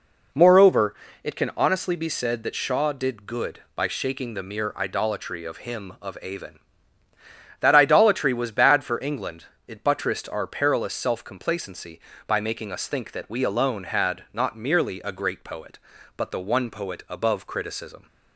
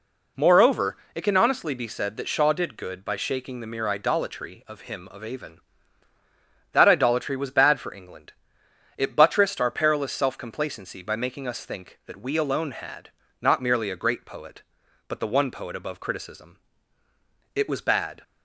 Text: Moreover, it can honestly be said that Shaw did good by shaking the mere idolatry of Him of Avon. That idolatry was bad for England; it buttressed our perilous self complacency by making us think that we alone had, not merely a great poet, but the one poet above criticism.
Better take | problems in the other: first | goes on to say "It was bad"; noticeable; from 17.5 s on; 0.68 s long

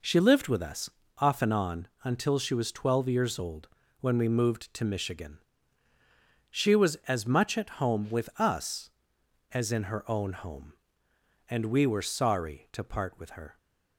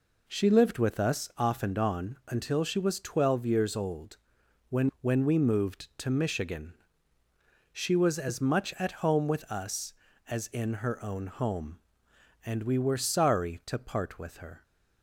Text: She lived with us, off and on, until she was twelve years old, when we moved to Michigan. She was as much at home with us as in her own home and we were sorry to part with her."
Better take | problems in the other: first | says "when" twice; at 5.0 s

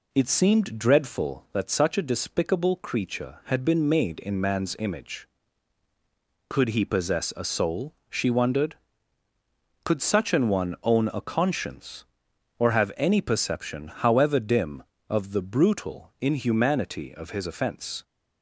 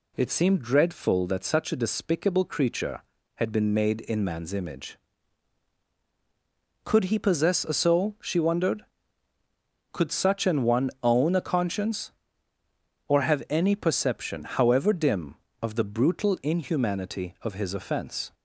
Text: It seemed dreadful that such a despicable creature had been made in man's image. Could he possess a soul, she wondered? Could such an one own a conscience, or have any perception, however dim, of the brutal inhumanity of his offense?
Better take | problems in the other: second | starts louder than the rest; slight; until 1.3 s; 3 dB

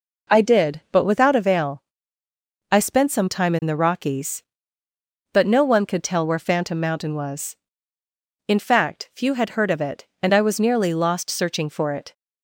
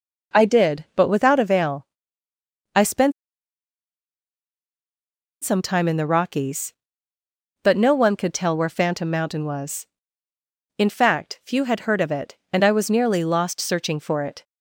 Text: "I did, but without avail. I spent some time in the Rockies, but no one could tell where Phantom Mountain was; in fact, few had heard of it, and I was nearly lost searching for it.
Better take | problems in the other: first | pauses between "spent" and "some"; strong; at 3.1 s; 2.3 s long

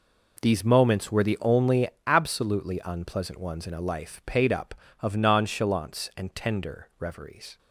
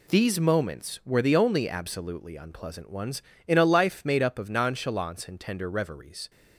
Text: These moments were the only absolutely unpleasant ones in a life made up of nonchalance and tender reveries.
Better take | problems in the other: second | pauses between "only" and "absolutely"; slight; at 1.8 s; 0.18 s long // says "paid" for "made"; at 4.2 s

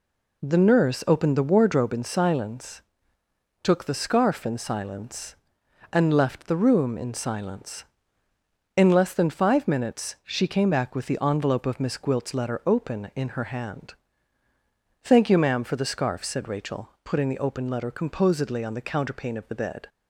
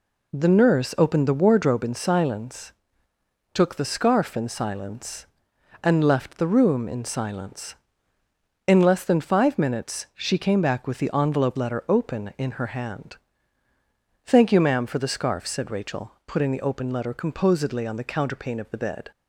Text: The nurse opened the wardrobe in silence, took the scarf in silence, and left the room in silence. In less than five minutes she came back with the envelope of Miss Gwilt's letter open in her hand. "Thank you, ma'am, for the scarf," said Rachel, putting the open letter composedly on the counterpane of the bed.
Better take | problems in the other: first | skips "of Miss Gwilt's"; at 11.5 s

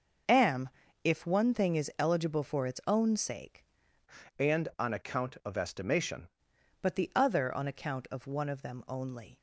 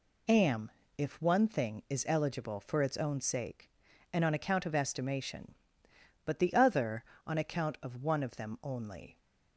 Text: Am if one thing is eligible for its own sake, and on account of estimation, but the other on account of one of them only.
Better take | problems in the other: second | pauses between "Am" and "if"; slight; at 0.6 s; 0.34 s long; slight in the second // changes voice from "and" to "estimation"; from 4.3 to 6.2 s; 1.9 s long

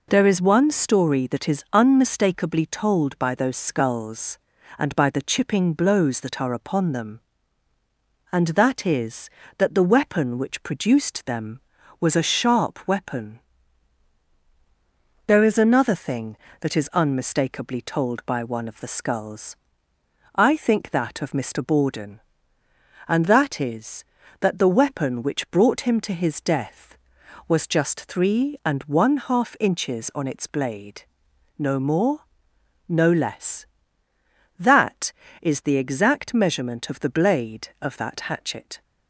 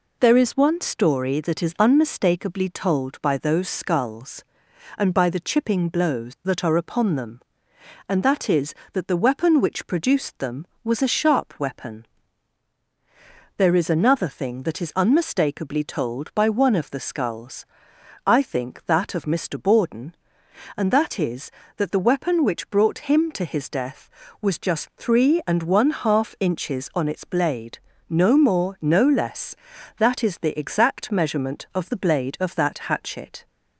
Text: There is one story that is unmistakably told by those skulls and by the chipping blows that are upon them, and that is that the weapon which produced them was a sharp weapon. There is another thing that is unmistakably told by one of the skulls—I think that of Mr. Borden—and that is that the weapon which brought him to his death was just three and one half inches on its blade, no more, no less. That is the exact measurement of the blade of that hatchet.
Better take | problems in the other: neither | none

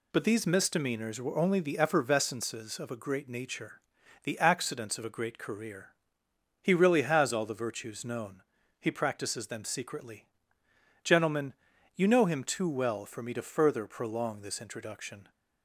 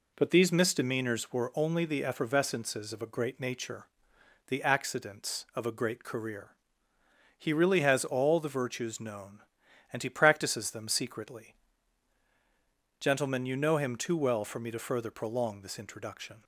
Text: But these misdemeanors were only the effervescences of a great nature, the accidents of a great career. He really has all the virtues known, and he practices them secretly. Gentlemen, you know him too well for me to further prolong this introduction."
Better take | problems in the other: second | skips "and"; at 8.6 s

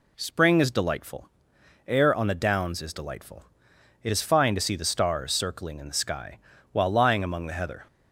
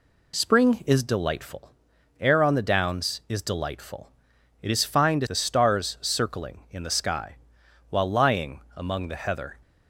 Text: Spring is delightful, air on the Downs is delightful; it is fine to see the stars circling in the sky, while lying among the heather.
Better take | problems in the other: first | skips "see"; at 5.2 s // pauses between "lying" and "among"; slight; at 8.5 s; 0.16 s long

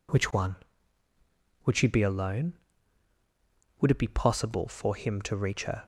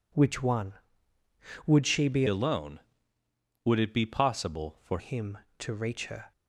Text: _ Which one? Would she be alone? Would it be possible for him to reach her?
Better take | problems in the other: first | changes voice from "alone" to "for"; from 2.2 to 4.9 s; 2.7 s long

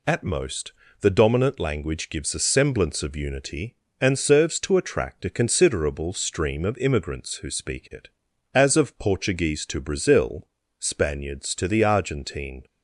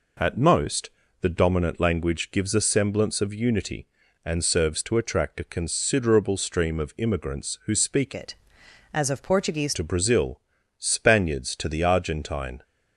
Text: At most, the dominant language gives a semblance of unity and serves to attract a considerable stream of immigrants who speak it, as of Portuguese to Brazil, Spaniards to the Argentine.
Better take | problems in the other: first | changes voice from "it" to "Portuguese"; from 8.1 to 9.7 s; 1.6 s long

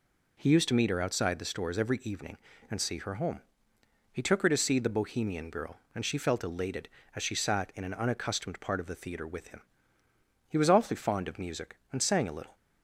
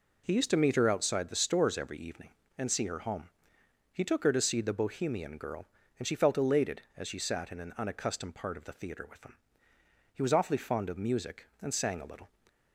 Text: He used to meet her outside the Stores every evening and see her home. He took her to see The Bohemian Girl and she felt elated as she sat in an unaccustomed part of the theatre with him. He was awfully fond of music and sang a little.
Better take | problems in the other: neither | none

